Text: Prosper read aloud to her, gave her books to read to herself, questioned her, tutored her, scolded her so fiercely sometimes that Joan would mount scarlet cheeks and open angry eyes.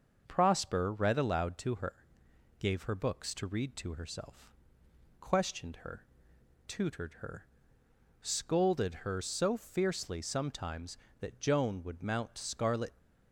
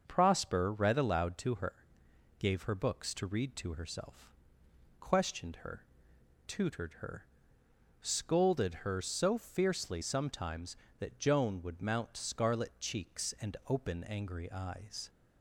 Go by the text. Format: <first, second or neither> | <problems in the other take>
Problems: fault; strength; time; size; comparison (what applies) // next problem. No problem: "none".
second | starts louder than the rest; until 1.2 s; 6.5 dB; also in the second // stops before "cheeks and open angry eyes"; at 12.9 s